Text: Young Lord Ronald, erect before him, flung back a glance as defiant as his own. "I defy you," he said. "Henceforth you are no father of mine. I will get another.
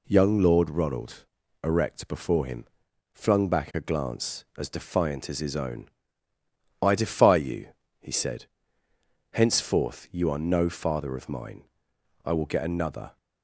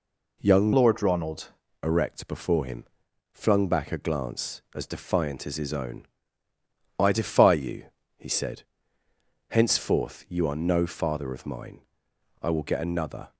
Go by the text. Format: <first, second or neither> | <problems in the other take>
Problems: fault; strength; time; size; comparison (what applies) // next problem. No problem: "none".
first | changes voice from "Lord" to "Ronald"; from 0.7 to 1.4 s; 0.7 s long